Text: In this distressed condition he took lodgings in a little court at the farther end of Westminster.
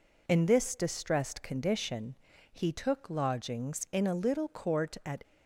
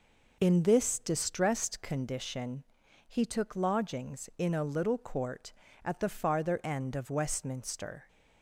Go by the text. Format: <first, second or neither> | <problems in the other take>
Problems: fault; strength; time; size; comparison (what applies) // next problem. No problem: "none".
second | pauses between "condition" and "he"; at 2.1 s; 0.38 s long; noticeable in the second // stops before "the farther end of Westminster"; at 5.2 s